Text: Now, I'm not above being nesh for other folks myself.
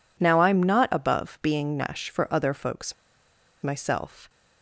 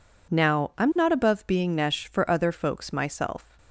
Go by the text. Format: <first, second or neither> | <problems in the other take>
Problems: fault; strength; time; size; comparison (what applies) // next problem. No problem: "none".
second | pauses between "folks" and "myself"; noticeable; at 2.9 s; 0.69 s long